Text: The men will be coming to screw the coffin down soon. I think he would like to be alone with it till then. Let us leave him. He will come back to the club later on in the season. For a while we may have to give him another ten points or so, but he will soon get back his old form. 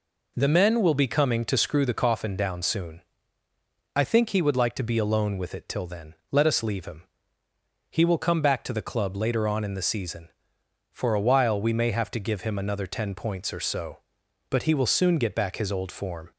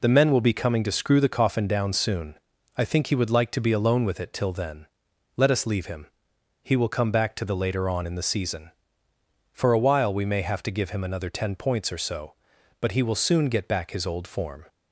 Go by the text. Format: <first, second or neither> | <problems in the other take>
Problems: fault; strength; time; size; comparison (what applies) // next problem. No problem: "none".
first | skips "club"; at 7.5 s